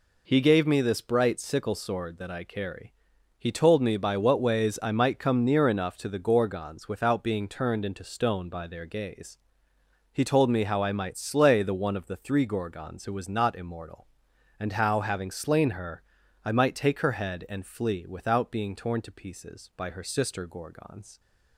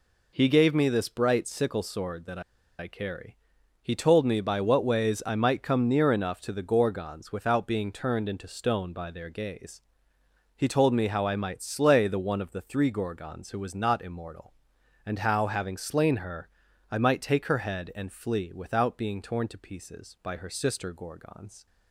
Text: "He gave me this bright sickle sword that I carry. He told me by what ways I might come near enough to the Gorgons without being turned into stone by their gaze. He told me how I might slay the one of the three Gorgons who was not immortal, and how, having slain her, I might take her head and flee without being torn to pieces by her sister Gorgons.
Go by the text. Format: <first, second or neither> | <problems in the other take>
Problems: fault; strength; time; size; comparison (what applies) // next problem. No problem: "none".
first | pauses between "that" and "I"; at 2.3 s; 0.39 s long